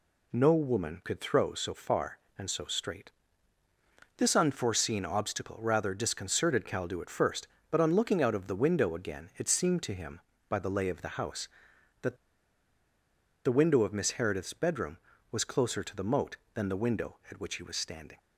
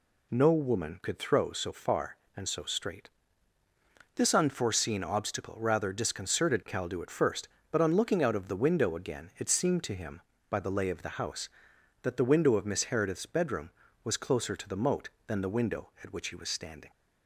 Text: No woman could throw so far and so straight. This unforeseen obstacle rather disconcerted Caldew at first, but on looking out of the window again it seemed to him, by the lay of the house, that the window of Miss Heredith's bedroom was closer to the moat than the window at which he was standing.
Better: second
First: pauses between "that" and "the"; strong; at 12.1 s; 1.2 s long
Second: none

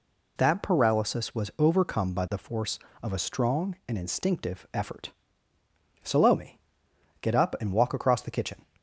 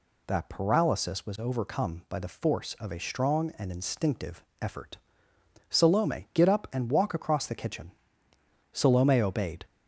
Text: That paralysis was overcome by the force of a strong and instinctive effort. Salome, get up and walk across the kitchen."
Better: first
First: none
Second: pauses between "instinctive" and "effort"; slight; at 4.4 s; 0.20 s long // goes on to say "Salome obeyed"; noticeable; from 8.7 s on; 0.94 s long

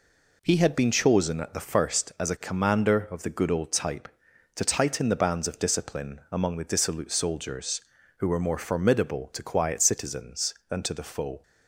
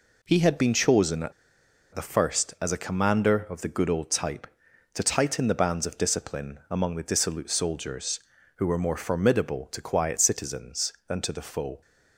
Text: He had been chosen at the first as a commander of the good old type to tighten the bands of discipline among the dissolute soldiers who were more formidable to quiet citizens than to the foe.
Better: first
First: none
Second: pauses between "at" and "the"; noticeable; at 1.3 s; 0.61 s long

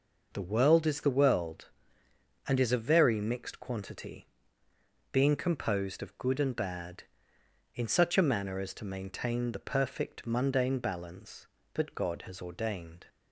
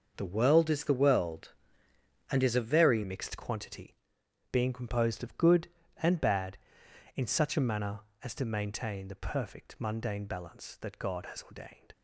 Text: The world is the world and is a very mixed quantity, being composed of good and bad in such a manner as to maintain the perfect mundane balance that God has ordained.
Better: first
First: none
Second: starts louder than the rest; until 1.1 s; 6.5 dB // changes voice at "mixed"; from 3.0 s on; 8.9 s long

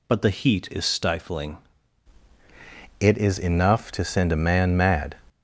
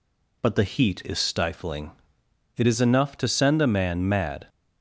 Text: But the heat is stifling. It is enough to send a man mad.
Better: second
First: changes voice at "It"; from 2.9 s on; 2.2 s long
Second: none

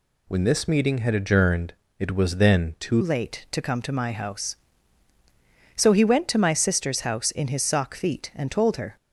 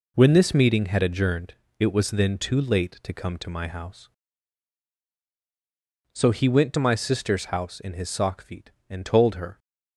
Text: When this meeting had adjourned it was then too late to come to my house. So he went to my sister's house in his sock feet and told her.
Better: second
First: pauses between "adjourned" and "it"; slight; at 1.7 s; 0.26 s long // changes voice at "late"; from 3.0 s on; 5.9 s long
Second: pauses between "adjourned" and "it"; slight; at 1.5 s; 0.26 s long

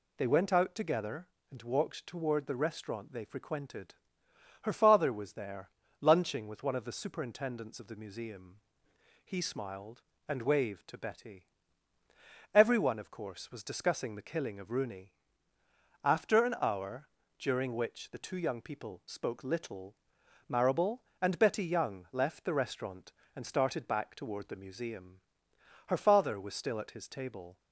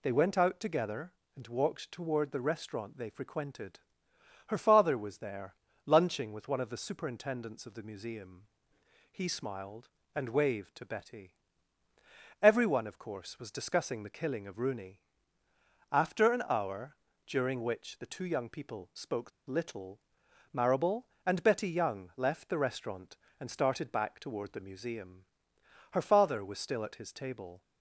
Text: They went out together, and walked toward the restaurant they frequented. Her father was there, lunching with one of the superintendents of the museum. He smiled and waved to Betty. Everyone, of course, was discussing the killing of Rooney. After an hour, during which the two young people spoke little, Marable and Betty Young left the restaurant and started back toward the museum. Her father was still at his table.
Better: first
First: none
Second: pauses between "spoke" and "little"; slight; at 19.3 s; 0.16 s long

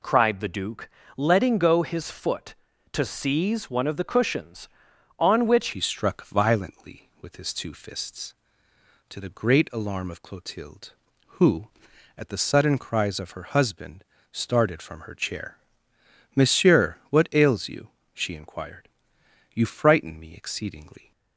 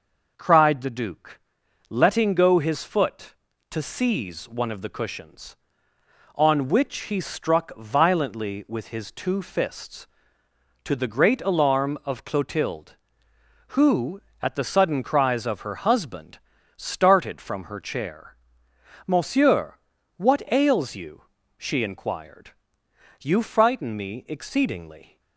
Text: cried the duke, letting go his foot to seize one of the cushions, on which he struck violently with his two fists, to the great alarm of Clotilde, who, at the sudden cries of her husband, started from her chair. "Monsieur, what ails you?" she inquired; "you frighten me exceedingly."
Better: second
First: changes voice at "he"; from 5.7 s on; 15.4 s long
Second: none

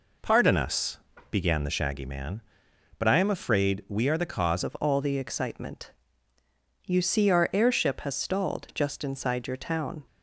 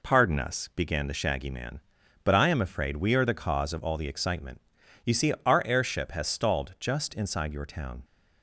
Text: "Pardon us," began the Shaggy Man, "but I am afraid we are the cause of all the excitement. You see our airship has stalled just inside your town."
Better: second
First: changes voice at "of"; from 4.6 s on; 5.4 s long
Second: none

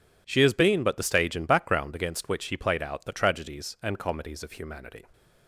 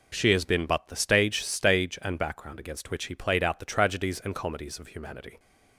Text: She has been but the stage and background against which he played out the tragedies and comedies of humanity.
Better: first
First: none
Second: says "stage" twice; at 1.4 s

